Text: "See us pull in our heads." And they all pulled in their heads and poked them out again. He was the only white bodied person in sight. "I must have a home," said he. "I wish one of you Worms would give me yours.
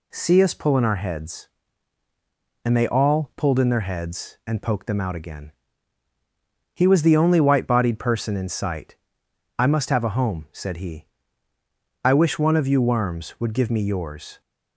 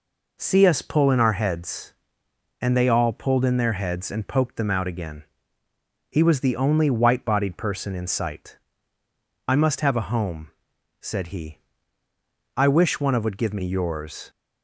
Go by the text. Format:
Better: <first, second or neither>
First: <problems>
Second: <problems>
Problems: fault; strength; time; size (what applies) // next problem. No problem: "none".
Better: first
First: none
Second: skips "you Worms"; at 13.2 s